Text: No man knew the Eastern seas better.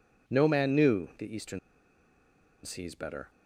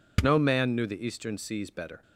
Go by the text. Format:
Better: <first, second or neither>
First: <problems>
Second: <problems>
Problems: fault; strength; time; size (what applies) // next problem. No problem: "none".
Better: second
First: pauses between "Eastern" and "seas"; at 1.5 s; 1.0 s long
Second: none